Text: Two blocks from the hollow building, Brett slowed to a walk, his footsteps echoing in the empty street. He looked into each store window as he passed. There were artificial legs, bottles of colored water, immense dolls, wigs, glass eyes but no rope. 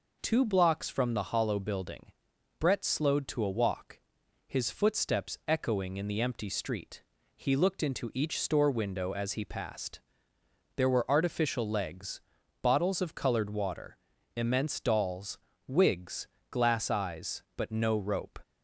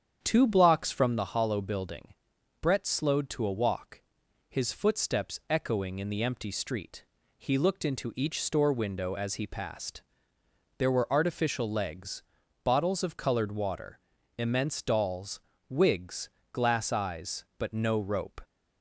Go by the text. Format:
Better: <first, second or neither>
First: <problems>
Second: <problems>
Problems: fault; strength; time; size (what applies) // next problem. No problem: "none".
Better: first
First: none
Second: starts louder than the rest; strong; until 1.2 s; 8 dB